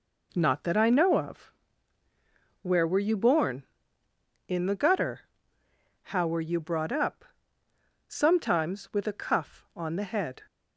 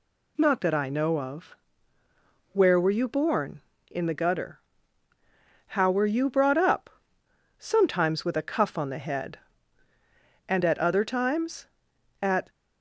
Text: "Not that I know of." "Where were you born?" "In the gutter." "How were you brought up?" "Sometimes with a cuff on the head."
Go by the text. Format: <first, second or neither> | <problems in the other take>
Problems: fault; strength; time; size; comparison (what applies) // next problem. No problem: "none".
first | goes on to say "And at other times At"; strong; from 10.4 s on; 2.0 s long